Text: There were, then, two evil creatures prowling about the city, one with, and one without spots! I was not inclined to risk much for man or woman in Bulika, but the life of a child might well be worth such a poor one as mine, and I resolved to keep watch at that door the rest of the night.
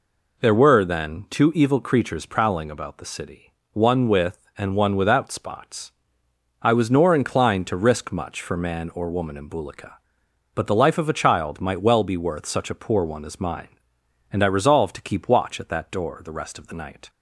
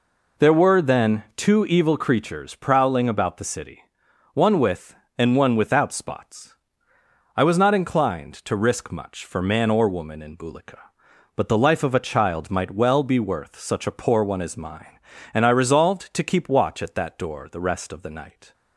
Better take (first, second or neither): second